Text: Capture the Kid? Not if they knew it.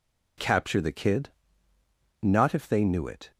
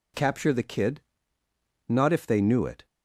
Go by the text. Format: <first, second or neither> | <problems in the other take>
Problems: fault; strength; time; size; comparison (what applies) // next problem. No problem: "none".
neither | none